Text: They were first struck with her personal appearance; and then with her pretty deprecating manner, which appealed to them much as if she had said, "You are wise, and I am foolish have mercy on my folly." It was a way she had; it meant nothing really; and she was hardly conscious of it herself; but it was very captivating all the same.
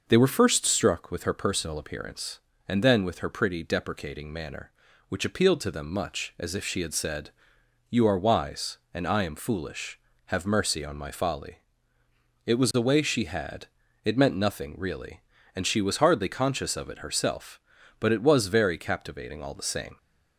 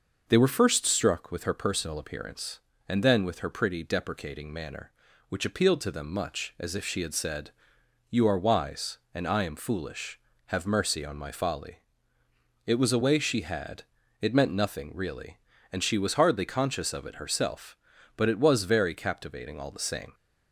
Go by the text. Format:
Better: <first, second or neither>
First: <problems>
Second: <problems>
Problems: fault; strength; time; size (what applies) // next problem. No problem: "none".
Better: neither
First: none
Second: none